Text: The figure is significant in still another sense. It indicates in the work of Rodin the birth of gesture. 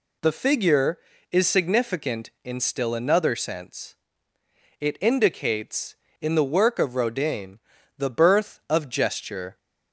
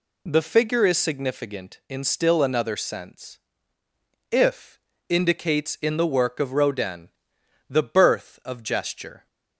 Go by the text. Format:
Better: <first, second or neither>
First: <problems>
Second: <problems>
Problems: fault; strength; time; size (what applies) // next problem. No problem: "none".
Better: first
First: pauses between "Rodin" and "the"; at 7.5 s; 0.38 s long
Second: says "If" for "It"; at 4.2 s // pauses between "Rodin" and "the"; noticeable; at 7.1 s; 0.58 s long